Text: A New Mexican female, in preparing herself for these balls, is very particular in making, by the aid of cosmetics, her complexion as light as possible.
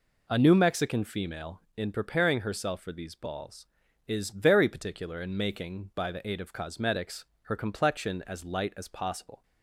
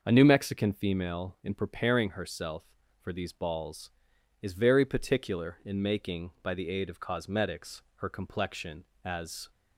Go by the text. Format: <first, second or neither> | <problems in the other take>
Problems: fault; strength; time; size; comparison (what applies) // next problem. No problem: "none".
first | starts louder than the rest; until 1.0 s; 6.5 dB // stops before "light as possible"; at 9.5 s